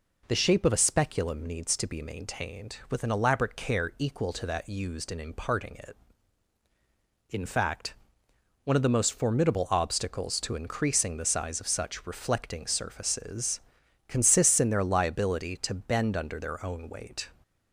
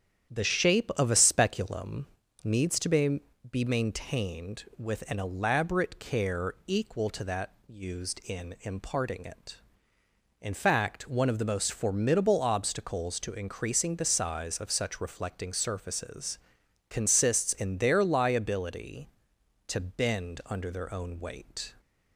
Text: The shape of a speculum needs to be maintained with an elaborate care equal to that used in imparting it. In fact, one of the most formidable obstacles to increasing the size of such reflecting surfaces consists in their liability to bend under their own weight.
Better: first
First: pauses between "surfaces" and "consists"; noticeable; at 13.6 s; 0.48 s long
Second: starts louder than the rest; strong; until 1.3 s; 9 dB // pauses between "speculum" and "needs"; slight; at 2.0 s; 0.36 s long // says "be" twice; at 3.5 s // pauses between "that" and "used"; slight; at 7.5 s; 0.16 s long // pauses between "surfaces" and "consists"; noticeable; at 16.3 s; 0.50 s long

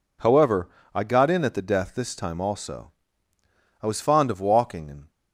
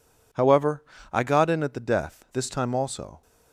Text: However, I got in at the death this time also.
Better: second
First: goes on to say "I was fond of walking and"; noticeable; from 3.8 s on; 1.2 s long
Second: none

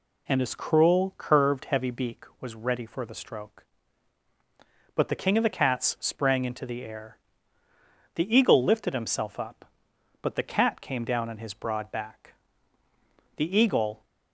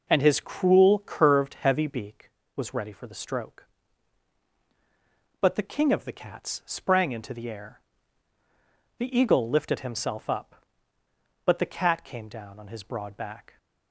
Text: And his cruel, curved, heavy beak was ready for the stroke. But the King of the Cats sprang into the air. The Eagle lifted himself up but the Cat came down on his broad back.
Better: second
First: goes on to say "The Eagle"; noticeable; from 13.3 s on; 0.66 s long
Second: none

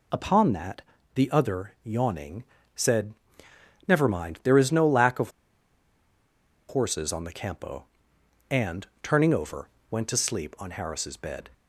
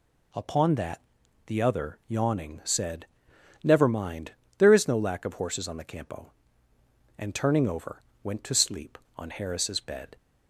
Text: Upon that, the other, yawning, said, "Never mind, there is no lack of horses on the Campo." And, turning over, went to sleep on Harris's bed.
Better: second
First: pauses between "of" and "horses"; strong; at 5.3 s; 1.3 s long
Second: none

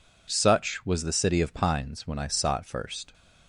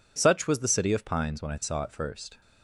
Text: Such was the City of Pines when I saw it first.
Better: neither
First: none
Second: none

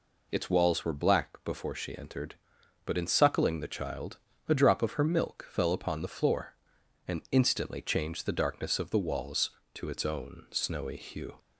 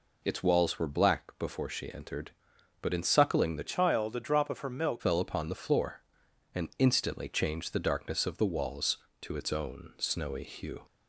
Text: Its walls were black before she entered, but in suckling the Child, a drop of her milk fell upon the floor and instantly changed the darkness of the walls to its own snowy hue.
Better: first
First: none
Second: changes voice from "Child" to "milk"; from 3.6 to 5.0 s; 1.4 s long

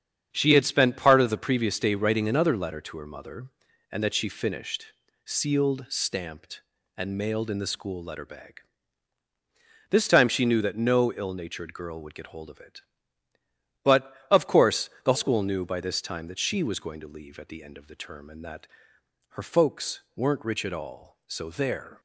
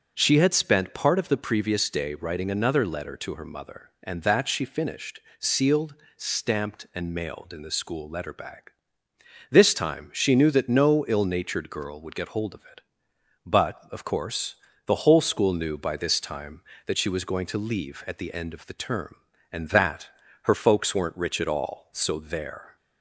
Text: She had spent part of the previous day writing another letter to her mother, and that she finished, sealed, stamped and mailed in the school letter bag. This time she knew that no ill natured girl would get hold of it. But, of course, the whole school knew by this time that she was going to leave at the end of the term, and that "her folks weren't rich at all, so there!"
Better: second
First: starts louder than the rest; strong; until 1.3 s; 8 dB // skips "whole"; at 15.1 s // pauses between "that" and "her"; noticeable; at 18.6 s; 0.66 s long // pauses between "folks" and "weren't"; slight; at 19.9 s; 0.16 s long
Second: starts louder than the rest; strong; until 1.1 s; 7.5 dB // pauses between "that" and "her"; slight; at 20.0 s; 0.32 s long

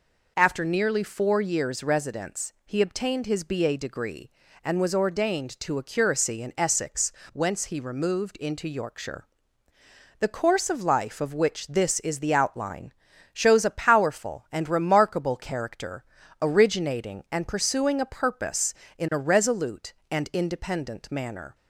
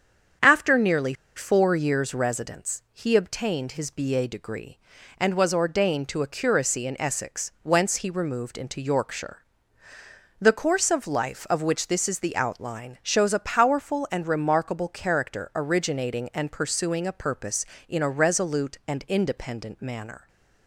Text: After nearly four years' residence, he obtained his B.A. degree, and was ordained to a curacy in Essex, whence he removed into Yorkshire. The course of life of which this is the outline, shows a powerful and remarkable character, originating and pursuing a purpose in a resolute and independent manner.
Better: first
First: none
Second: starts louder than the rest; strong; until 1.6 s; 8 dB // pauses between "nearly" and "four"; slight; at 1.1 s; 0.23 s long

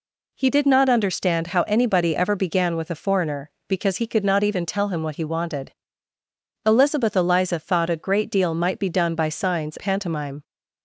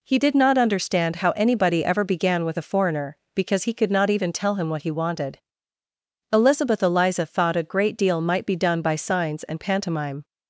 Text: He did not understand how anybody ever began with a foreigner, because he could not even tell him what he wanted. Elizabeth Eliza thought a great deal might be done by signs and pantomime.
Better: second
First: skips "and"; at 9.7 s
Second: none

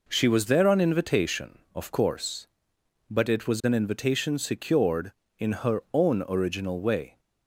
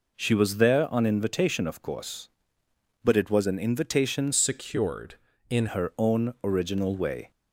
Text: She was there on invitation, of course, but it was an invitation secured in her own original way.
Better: first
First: none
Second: changes voice from "secured" to "in"; from 4.3 to 5.6 s; 1.3 s long

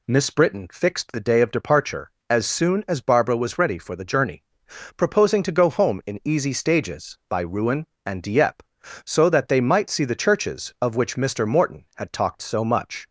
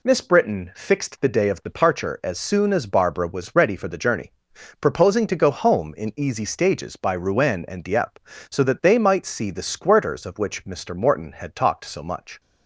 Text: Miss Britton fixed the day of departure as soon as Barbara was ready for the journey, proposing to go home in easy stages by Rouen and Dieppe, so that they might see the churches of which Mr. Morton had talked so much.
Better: first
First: none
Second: says "squirters" for "churches"; at 9.6 s

